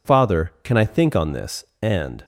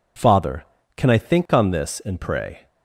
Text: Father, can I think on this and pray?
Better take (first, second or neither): second